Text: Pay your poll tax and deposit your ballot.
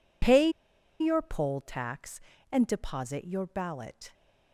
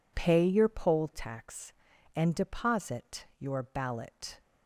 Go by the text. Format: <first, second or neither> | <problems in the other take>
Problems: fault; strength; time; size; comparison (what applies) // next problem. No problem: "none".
second | pauses between "Pay" and "your"; noticeable; at 0.4 s; 0.51 s long